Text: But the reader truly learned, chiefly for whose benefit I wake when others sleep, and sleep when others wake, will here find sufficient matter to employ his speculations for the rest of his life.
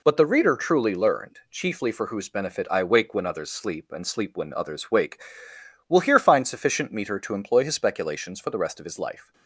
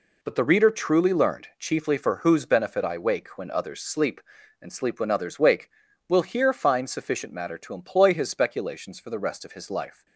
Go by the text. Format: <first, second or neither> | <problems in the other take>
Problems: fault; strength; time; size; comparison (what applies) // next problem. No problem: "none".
second | says "meter" for "matter"; at 6.9 s